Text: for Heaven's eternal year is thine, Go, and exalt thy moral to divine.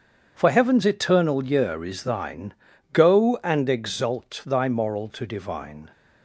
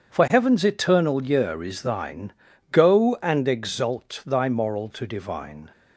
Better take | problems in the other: neither | starts louder than the rest; strong; the same in both

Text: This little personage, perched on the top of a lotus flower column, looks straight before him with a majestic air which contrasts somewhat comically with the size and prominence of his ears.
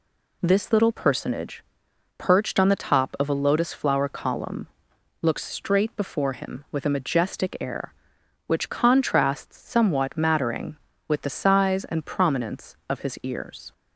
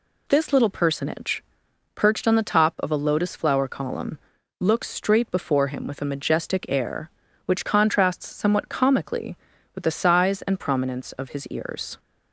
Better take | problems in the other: second | says "mattering" for "comically"; at 10.1 s

